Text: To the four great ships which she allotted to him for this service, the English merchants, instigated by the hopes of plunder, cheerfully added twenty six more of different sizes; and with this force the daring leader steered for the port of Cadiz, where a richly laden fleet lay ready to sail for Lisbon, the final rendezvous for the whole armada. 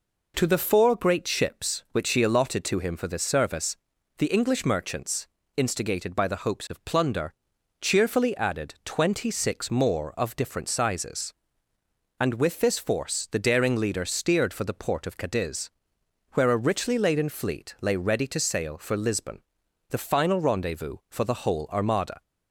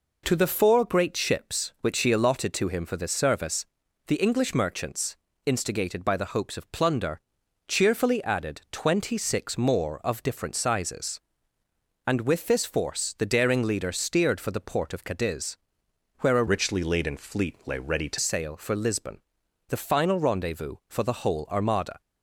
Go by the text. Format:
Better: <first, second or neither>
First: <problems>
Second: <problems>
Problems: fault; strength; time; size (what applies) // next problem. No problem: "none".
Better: first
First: none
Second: changes voice from "richly" to "to"; from 16.4 to 18.1 s; 1.7 s long